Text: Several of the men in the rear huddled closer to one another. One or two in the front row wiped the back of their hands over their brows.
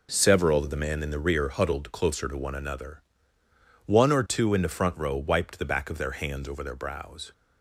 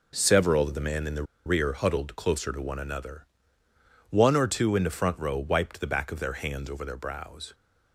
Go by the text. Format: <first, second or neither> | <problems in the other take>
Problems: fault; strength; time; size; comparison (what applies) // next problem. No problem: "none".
first | pauses between "the" and "rear"; slight; at 1.2 s; 0.21 s long